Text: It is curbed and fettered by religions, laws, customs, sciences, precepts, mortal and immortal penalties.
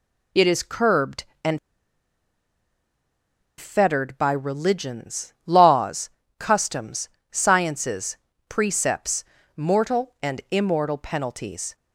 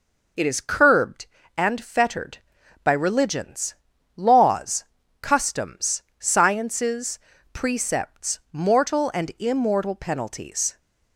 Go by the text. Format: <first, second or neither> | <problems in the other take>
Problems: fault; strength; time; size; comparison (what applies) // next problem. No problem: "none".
second | pauses between "and" and "fettered"; strong; at 1.5 s; 1.9 s long